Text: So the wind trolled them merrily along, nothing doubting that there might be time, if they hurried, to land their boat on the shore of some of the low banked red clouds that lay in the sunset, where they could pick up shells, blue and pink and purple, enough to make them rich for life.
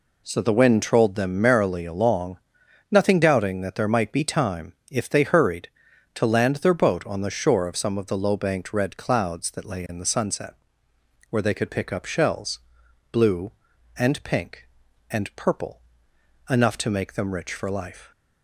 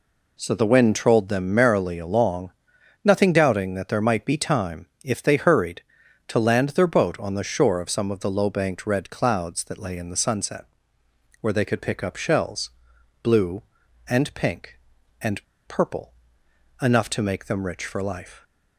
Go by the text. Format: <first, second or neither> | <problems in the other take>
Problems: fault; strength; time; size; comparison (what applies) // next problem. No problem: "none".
first | pauses between "and" and "purple"; slight; at 15.4 s; 0.25 s long